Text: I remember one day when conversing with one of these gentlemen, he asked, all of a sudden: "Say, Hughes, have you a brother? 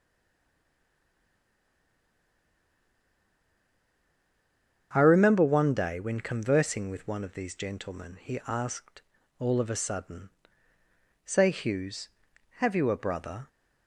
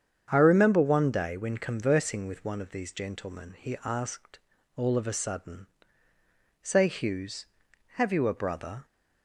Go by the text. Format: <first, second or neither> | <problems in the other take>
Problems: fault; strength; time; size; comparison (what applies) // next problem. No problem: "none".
second | stays silent before the first word; strong; until 4.9 s; 4.9 s long // starts louder than the rest; strong; until 5.9 s; 8 dB; strong in the second